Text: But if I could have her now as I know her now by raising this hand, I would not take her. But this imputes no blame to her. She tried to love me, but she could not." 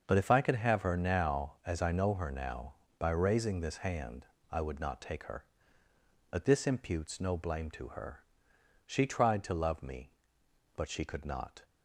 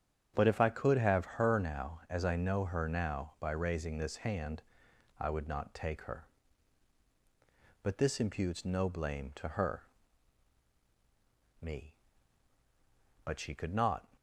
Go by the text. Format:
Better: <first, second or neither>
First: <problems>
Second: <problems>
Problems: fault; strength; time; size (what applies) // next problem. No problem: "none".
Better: first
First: starts louder than the rest; until 1.0 s; 6.5 dB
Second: starts louder than the rest; strong; until 1.3 s; 8.5 dB // skips "She tried to love"; at 10.7 s